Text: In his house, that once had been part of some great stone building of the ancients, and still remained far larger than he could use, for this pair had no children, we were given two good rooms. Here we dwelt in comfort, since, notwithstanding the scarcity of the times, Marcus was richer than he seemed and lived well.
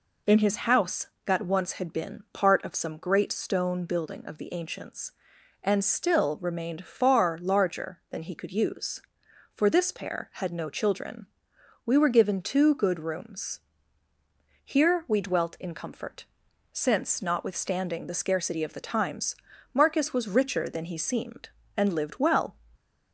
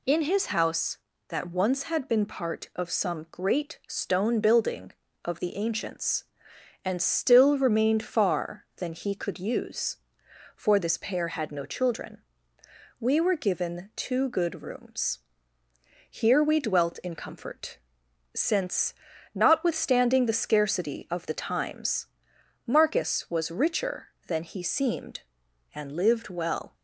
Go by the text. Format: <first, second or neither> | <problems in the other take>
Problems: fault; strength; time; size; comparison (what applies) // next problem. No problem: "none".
first | skips "larger"; at 8.7 s